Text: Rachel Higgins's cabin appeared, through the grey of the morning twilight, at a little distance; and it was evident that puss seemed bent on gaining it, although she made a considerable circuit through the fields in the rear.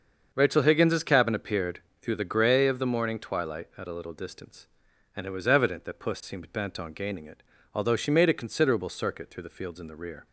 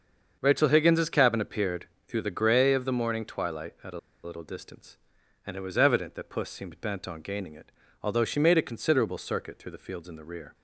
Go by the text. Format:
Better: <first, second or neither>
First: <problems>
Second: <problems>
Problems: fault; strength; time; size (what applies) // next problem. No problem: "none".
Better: first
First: starts louder than the rest; until 1.3 s; 6.5 dB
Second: starts louder than the rest; until 1.4 s; 6.5 dB // pauses between "a" and "little"; slight; at 3.9 s; 0.24 s long